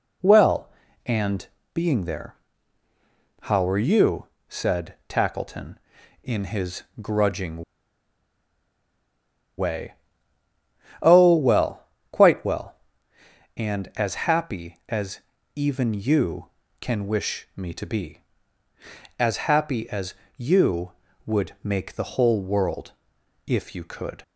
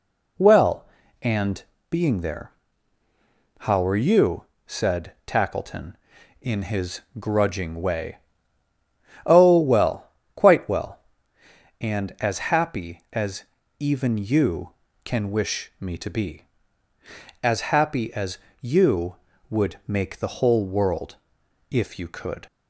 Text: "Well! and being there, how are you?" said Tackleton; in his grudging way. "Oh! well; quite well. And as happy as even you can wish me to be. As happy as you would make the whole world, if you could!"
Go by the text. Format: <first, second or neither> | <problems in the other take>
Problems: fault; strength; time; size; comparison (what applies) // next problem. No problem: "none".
second | pauses between "and" and "being"; slight; at 1.4 s; 0.26 s long; slight in the second // pauses between "his" and "grudging"; slight; at 6.8 s; 0.18 s long; slight in the second // pauses between "grudging" and "way"; strong; at 7.6 s; 1.9 s long // pauses between "as" and "even"; slight; at 15.2 s; 0.34 s long; slight in the second // pauses between "as" and "you"; slight; at 20.1 s; 0.22 s long; slight in the second